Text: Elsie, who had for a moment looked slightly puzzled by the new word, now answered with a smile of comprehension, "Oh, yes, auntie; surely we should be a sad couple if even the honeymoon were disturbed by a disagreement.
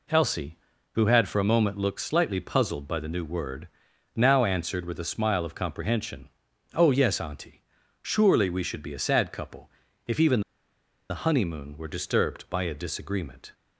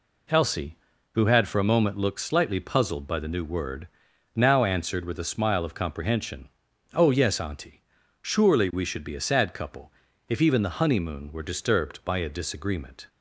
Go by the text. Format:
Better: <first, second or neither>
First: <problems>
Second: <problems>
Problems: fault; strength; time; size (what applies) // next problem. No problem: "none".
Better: second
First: pauses between "couple" and "if"; at 9.6 s; 0.38 s long // pauses between "even" and "the"; noticeable; at 10.4 s; 0.69 s long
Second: pauses between "couple" and "if"; at 9.9 s; 0.38 s long